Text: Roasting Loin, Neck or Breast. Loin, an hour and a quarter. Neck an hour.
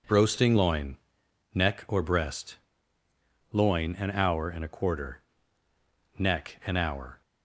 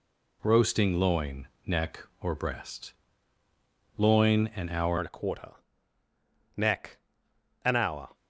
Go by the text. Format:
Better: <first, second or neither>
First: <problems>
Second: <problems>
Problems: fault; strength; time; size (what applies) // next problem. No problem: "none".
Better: first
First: none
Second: changes voice at "and"; from 4.9 s on; 3.2 s long // pauses between "Neck" and "an"; noticeable; at 6.9 s; 0.66 s long